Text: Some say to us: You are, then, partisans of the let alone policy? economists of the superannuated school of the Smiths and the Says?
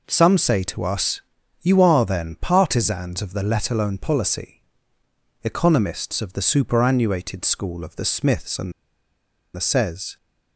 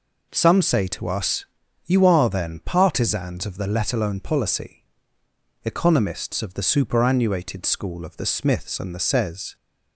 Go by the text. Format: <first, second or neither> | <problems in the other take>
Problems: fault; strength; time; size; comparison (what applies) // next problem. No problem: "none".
second | pauses between "and" and "the"; noticeable; at 8.7 s; 0.82 s long